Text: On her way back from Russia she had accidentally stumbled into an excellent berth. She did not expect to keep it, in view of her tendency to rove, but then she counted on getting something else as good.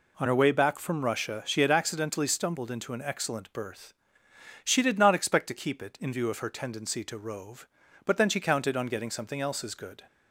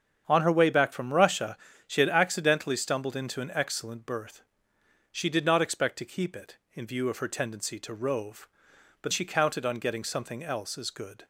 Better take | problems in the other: first | starts louder than the rest; strong; until 1.2 s; 7.5 dB // pauses between "Russia" and "she"; slight; at 1.5 s; 0.30 s long // skips "then"; at 9.1 s

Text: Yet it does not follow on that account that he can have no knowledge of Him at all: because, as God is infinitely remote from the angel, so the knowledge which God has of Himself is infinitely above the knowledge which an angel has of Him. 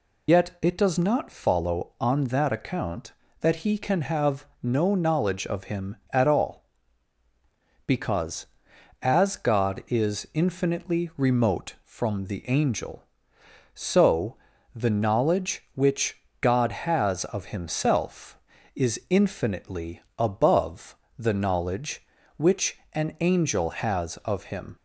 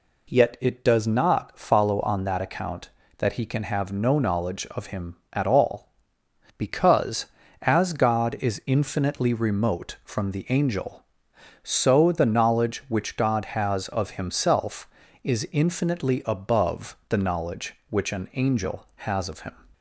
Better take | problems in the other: second | loses the start of "Yet"; at 0.2 s; 70 ms // pauses between "have" and "no"; slight; at 4.4 s; 0.16 s long // pauses between "so" and "the"; at 14.3 s; 0.40 s long // pauses between "which" and "God"; slight; at 16.1 s; 0.24 s long // pauses between "infinitely" and "above"; slight; at 20.0 s; 0.16 s long // pauses between "above" and "the"; slight; at 20.9 s; 0.22 s long // pauses between "which" and "an"; slight; at 22.7 s; 0.16 s long

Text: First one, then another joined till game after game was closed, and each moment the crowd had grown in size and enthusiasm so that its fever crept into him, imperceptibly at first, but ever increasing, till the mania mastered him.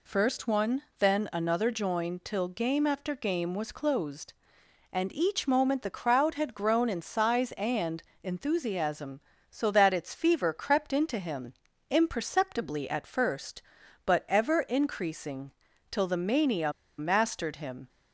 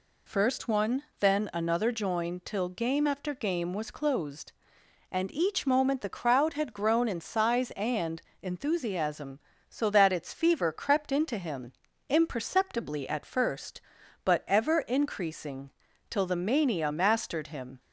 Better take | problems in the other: second | pauses between "and" and "enthusiasm"; slight; at 8.0 s; 0.18 s long; slight in the second // pauses between "mania" and "mastered"; slight; at 16.7 s; 0.26 s long

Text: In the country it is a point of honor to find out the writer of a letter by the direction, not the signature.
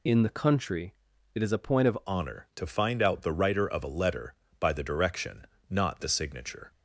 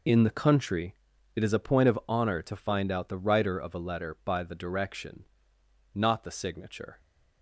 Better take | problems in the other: second | pauses between "country" and "it"; at 0.9 s; 0.40 s long; also in the second // changes voice at "honor"; from 2.0 s on; 4.7 s long

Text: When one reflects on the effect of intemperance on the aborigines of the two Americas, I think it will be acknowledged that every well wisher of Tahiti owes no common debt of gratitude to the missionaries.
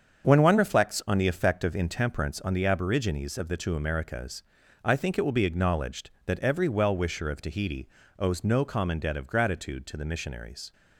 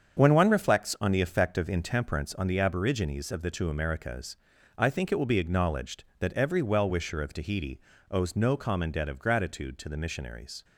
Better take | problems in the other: neither | starts louder than the rest; strong; the same in both // pauses between "Tahiti" and "owes"; slight; the same in both

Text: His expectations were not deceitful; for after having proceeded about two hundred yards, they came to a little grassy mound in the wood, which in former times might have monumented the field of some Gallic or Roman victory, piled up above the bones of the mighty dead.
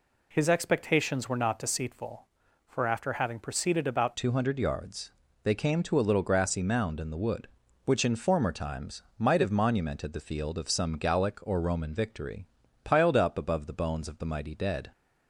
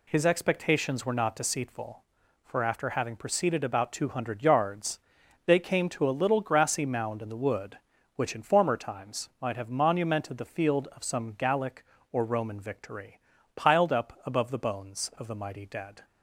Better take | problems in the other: second | changes voice at "two"; from 4.1 s on; 10.8 s long // pauses between "times" and "might"; slight; at 9.0 s; 0.16 s long

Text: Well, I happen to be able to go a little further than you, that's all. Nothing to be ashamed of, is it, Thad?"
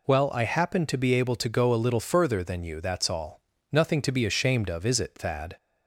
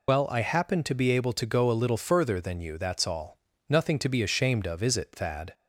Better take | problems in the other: first | loses the start of "Well"; at 0.0 s; 50 ms

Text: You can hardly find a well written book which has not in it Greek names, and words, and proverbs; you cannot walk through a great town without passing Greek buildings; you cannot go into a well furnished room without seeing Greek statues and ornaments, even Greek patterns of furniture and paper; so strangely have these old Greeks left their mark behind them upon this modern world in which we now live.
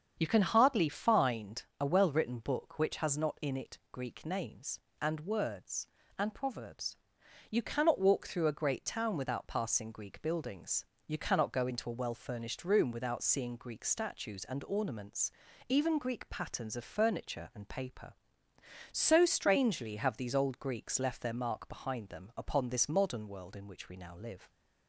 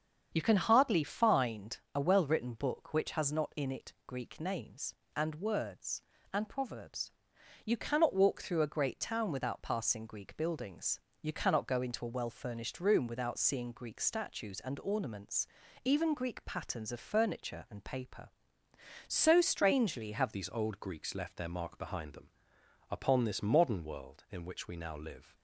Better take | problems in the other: first | starts louder than the rest; strong; until 1.3 s; 7.5 dB; strong in the first // pauses between "find" and "a"; slight; at 1.7 s; 0.16 s long; slight in the first // changes voice at "these"; from 20.3 s on; 5.0 s long // pauses between "them" and "upon"; noticeable; at 22.2 s; 0.62 s long

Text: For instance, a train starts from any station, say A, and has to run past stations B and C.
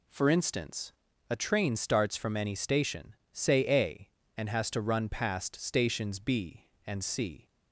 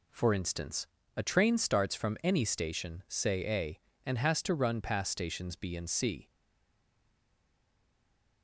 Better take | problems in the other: first | stays silent after the last word; from 6.2 s on; 2.2 s long

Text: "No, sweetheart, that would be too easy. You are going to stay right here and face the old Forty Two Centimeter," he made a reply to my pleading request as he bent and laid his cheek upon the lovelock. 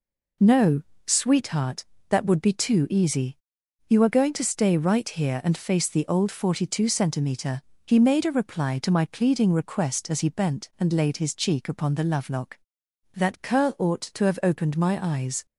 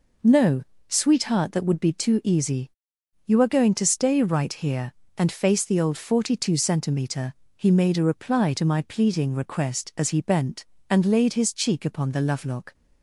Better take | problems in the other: second | goes on to say "That curl ought to have opened my eyes"; strong; from 13.1 s on; 2.3 s long

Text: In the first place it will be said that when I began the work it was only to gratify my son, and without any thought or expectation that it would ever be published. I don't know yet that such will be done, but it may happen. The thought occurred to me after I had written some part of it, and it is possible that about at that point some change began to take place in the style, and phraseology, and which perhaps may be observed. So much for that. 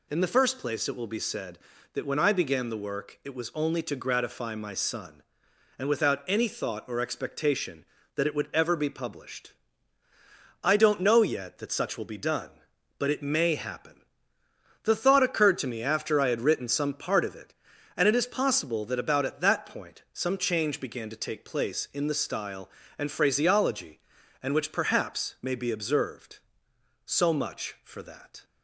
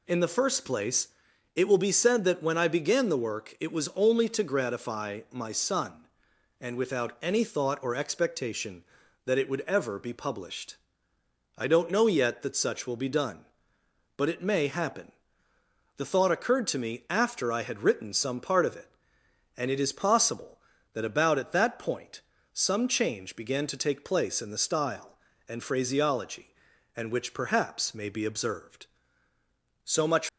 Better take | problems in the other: first | pauses between "place" and "it"; noticeable; at 1.0 s; 0.46 s long // pauses between "point" and "some"; slight; at 22.2 s; 0.32 s long // stops before "for that"; at 30.2 s

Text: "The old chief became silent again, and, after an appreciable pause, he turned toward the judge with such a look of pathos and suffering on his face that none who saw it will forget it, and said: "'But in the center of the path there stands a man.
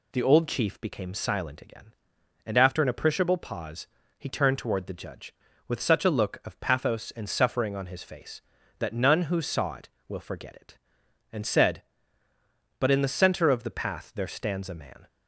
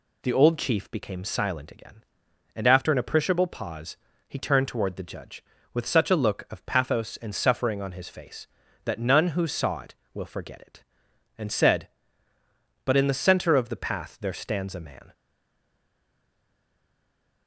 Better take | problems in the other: first | stays silent after the last word; from 15.1 s on; 2.3 s long

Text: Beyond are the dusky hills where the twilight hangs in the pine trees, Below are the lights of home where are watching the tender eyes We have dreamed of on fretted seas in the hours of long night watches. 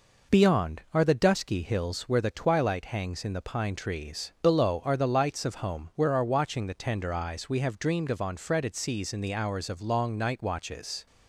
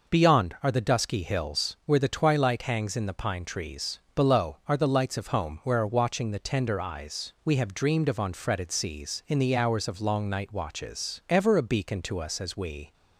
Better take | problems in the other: first | goes on to say "Ever a beacon to us as we"; from 11.2 s on; 1.6 s long

